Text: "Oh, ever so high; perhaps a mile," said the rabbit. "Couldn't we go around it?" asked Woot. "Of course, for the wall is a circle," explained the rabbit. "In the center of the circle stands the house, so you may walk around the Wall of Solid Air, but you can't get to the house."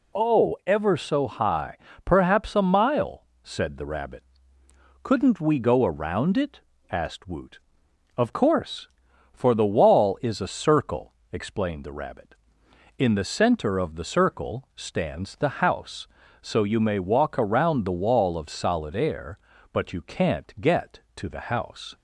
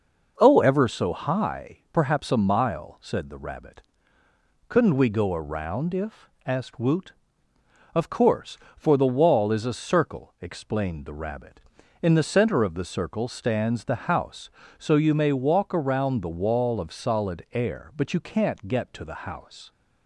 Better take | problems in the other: first | says "if" for "it"; at 5.9 s

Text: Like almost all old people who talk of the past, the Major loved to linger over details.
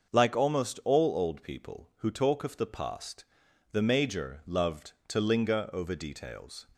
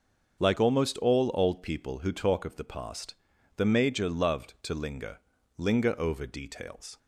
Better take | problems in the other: first | starts louder than the rest; until 1.4 s; 6.5 dB; also in the first // says "linger" twice; at 5.5 s

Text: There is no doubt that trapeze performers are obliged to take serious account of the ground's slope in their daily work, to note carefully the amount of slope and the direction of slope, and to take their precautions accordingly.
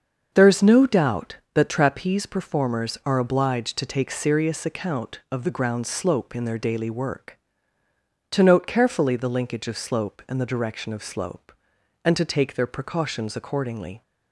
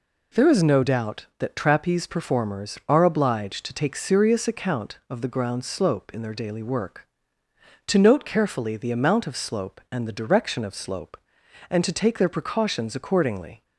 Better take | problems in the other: second | starts louder than the rest; until 1.3 s; 6.5 dB // says "linkage" for "amount"; at 9.2 s

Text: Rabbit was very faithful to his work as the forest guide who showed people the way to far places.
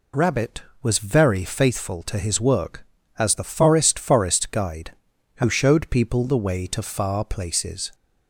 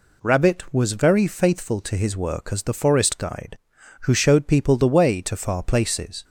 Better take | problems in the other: second | says "forest" twice; at 3.9 s

